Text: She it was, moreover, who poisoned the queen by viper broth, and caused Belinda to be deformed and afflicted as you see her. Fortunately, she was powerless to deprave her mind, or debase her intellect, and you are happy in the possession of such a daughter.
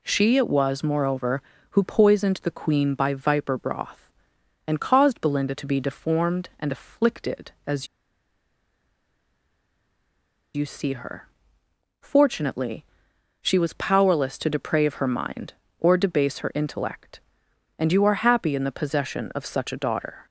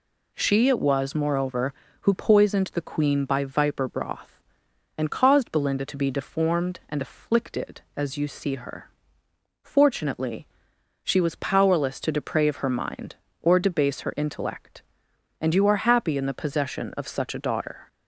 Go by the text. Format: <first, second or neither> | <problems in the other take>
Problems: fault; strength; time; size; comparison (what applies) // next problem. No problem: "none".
second | pauses between "as" and "you"; strong; at 7.8 s; 2.6 s long